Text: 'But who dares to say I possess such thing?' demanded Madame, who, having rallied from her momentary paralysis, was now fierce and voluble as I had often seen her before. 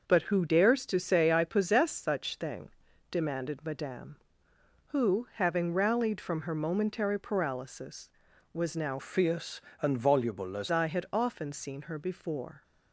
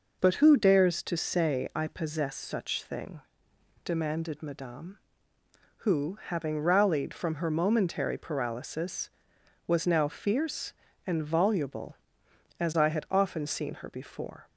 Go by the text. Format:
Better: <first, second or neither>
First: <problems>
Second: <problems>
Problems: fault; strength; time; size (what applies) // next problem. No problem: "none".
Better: second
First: changes voice from "fierce" to "as"; from 8.9 to 10.6 s; 1.7 s long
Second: none